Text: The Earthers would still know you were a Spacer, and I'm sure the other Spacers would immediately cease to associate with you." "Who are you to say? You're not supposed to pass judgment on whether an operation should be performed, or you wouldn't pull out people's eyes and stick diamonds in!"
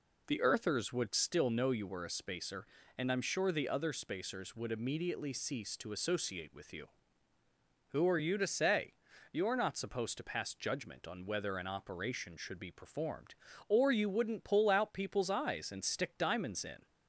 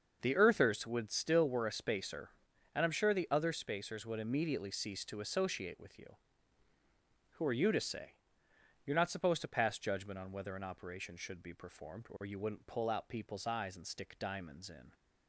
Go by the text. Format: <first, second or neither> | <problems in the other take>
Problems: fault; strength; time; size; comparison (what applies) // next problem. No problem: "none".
first | starts louder than the rest; until 1.2 s; 6.5 dB // skips "know you"; at 1.4 s